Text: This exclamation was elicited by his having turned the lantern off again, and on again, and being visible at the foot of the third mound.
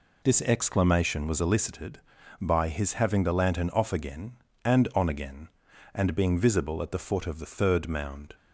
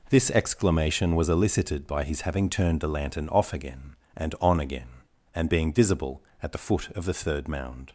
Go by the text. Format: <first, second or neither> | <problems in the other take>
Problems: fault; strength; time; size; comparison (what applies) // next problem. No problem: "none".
second | skips "turned"; at 3.2 s